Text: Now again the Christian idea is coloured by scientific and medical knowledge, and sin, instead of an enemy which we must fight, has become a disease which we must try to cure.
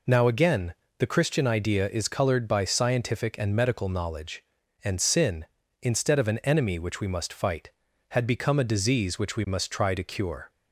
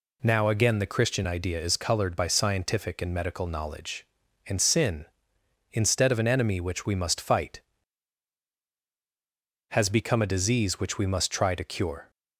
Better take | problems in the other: second | pauses between "again" and "the"; slight; at 0.7 s; 0.24 s long // says "had" for "has"; at 8.0 s

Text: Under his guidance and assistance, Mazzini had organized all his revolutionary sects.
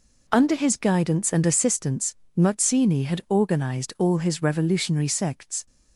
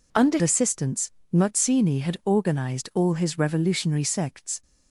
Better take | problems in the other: first | skips "his guidance and"; at 0.3 s

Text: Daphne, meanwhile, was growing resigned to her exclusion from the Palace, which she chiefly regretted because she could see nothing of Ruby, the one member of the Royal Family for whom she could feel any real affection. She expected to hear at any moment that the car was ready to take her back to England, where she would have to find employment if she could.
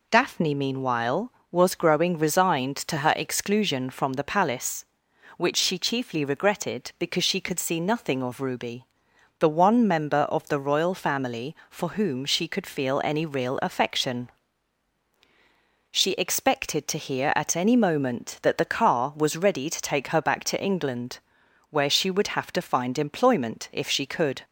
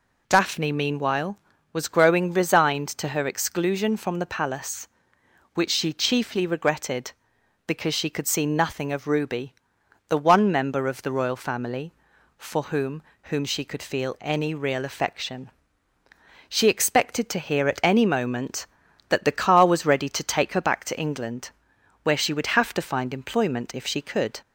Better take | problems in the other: first | says "whom" twice; at 13.2 s

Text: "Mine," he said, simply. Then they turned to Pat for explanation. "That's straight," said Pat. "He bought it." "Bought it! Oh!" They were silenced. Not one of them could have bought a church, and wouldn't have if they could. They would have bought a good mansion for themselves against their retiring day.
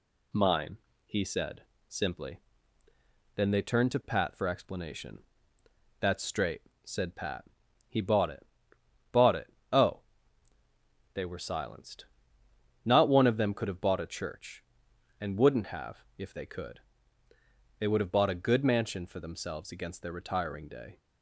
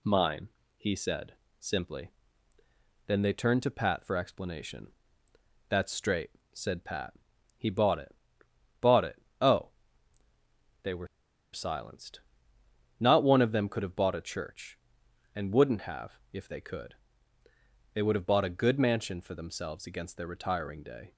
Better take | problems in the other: first | pauses between "were" and "silenced"; noticeable; at 11.0 s; 0.46 s long

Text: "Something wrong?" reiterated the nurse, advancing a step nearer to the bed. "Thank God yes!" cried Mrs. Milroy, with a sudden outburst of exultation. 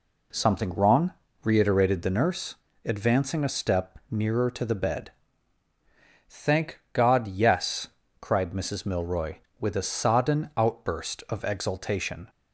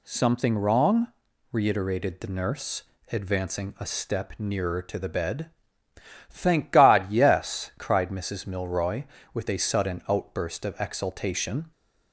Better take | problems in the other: second | says "sodden" for "sudden"; at 9.8 s

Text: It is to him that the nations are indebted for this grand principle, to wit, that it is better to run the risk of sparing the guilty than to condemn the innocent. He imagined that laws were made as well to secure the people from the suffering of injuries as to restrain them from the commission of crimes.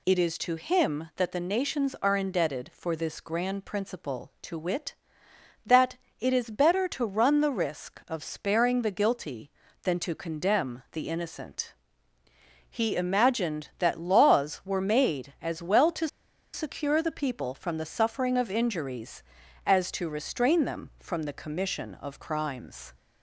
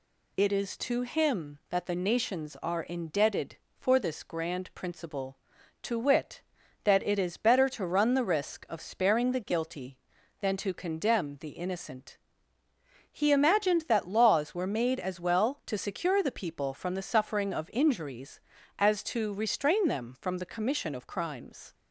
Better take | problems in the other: second | pauses between "that" and "it"; slight; at 5.9 s; 0.24 s long // pauses between "to" and "secure"; at 16.0 s; 0.45 s long

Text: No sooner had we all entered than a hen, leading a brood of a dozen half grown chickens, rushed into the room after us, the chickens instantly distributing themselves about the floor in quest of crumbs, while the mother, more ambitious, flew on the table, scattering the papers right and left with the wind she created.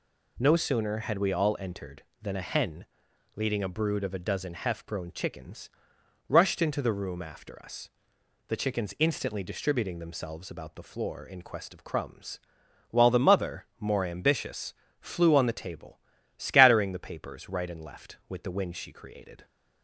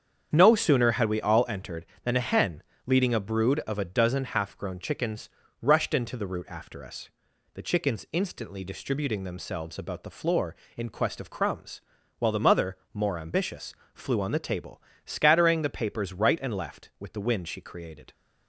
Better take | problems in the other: first | starts louder than the rest; strong; until 1.3 s; 7.5 dB // says "root" for "room"; at 6.2 s

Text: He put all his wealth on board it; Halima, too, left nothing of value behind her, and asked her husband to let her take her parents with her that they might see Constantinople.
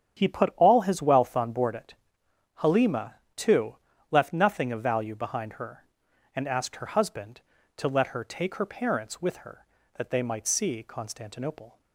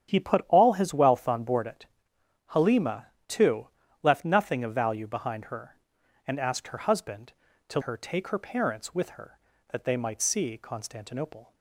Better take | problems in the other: first | starts louder than the rest; strong; until 1.1 s; 9 dB; strong in the first // skips "let"; at 7.8 s

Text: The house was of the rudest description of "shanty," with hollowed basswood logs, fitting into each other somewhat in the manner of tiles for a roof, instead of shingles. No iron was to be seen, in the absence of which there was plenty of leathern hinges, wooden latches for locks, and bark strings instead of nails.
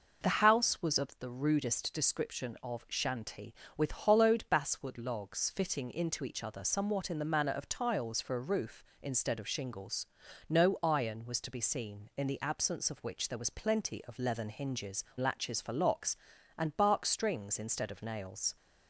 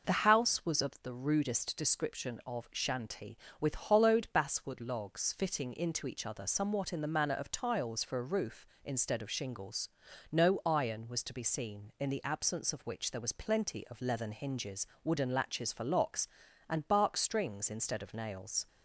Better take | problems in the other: second | skips "wooden"; at 15.1 s

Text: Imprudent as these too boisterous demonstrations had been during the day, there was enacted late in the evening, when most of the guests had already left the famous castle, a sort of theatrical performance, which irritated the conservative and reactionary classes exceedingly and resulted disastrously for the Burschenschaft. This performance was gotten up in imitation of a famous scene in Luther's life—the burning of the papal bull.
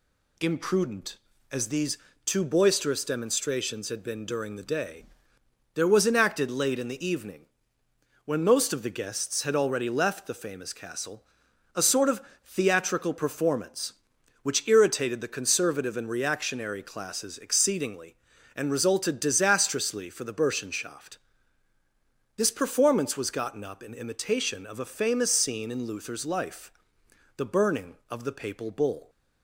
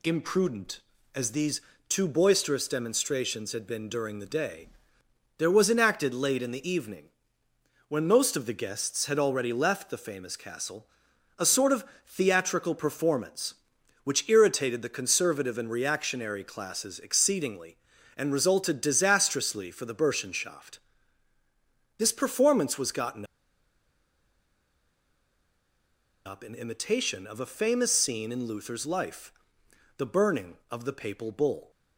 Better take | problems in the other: first | pauses between "these" and "too"; slight; at 1.6 s; 0.26 s long; slight in the first // pauses between "of" and "theatrical"; slight; at 11.8 s; 0.22 s long; slight in the first // pauses between "gotten" and "up"; strong; at 23.2 s; 3.0 s long

